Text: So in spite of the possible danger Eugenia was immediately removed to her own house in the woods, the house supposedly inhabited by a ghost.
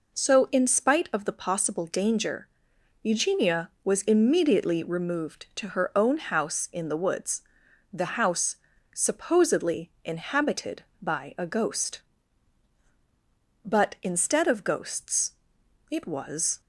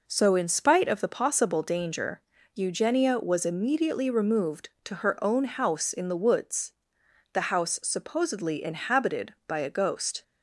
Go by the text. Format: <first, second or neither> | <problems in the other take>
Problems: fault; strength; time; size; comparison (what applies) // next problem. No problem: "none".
second | pauses between "danger" and "Eugenia"; noticeable; at 2.4 s; 0.54 s long; slight in the second // pauses between "house" and "supposedly"; at 8.5 s; 0.38 s long // goes on to say "But instead of ghosts it was"; strong; from 13.6 s on; 2.9 s long